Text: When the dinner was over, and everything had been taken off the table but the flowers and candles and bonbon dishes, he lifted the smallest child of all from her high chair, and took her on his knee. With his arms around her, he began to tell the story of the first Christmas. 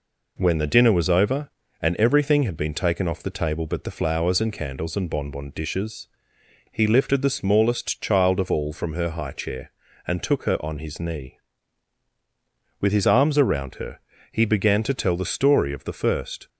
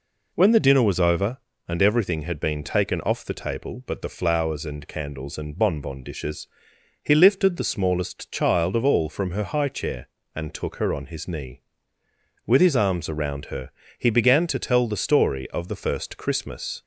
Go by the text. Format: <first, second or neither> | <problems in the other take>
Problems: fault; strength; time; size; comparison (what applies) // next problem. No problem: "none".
second | stops before "Christmas"; at 16.4 s